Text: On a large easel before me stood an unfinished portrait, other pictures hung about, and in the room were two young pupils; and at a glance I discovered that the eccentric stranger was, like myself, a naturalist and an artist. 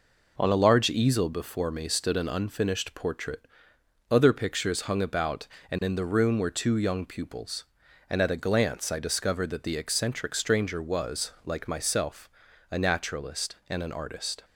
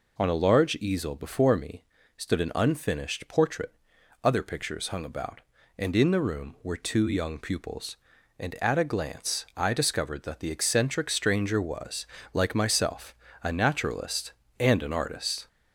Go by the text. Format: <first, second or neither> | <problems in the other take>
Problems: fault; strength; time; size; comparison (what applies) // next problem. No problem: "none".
first | gets louder; slight; throughout; 2.5 dB // pauses between "me" and "stood"; slight; at 1.8 s; 0.34 s long